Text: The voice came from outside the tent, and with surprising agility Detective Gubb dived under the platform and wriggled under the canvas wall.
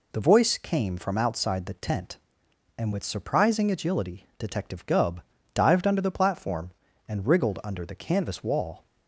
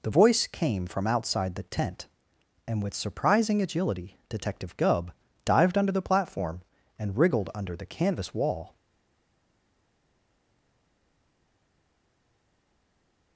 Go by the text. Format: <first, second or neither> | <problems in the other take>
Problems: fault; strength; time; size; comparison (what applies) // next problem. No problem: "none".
first | pauses between "Gubb" and "dived"; slight; at 5.1 s; 0.32 s long; slight in the first // stays silent after the last word; strong; from 8.7 s on; 4.6 s long